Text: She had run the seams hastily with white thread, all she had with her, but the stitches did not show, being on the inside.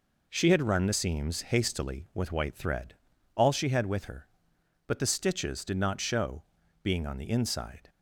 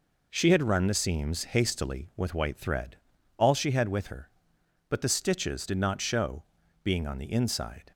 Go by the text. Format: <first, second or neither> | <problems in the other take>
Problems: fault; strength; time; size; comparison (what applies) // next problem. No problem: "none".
neither | none